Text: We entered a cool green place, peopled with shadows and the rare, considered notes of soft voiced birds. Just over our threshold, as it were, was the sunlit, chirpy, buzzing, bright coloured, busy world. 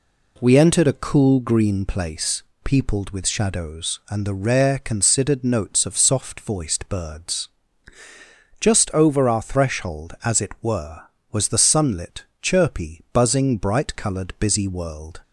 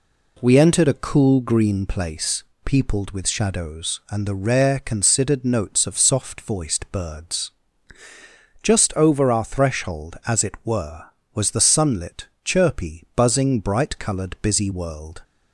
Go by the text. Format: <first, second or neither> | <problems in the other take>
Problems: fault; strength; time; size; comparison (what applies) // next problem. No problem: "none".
neither | none